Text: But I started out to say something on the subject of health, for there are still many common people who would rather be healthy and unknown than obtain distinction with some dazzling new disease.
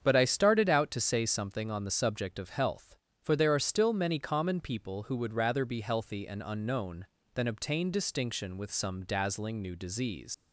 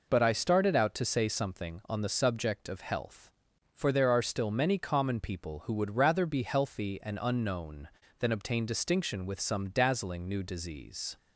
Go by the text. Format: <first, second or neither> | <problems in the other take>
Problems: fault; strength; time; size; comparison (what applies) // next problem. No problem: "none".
second | starts louder than the rest; strong; until 1.0 s; 7.5 dB // leaves "disease" unfinished; at 10.3 s; 125 ms